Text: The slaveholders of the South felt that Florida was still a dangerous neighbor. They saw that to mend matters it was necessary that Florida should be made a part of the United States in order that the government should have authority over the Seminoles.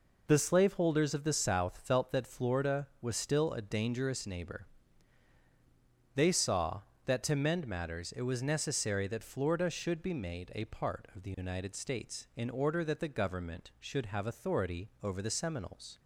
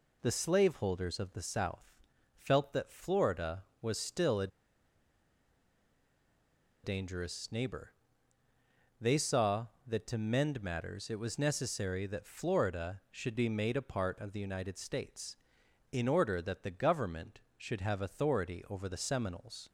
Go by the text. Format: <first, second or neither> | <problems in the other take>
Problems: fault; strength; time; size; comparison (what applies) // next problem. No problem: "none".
first | pauses between "South" and "felt"; at 1.9 s; 0.42 s long // pauses between "a" and "dangerous"; strong; at 4.4 s; 2.3 s long